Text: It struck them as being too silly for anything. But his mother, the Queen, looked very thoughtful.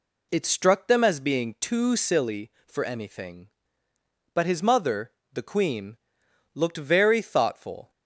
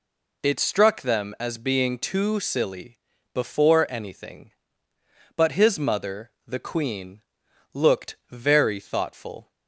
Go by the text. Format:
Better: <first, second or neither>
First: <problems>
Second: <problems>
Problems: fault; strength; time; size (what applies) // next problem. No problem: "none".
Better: first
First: none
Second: says "before" for "for"; at 3.3 s